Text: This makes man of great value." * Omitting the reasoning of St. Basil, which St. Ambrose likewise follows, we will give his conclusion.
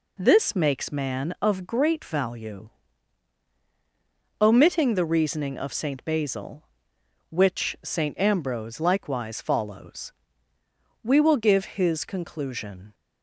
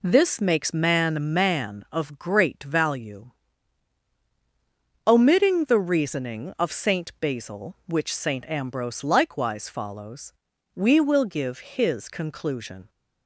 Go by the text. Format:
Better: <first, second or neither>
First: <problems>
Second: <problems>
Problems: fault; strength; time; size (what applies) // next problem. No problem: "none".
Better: first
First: none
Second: says "man" twice; at 1.3 s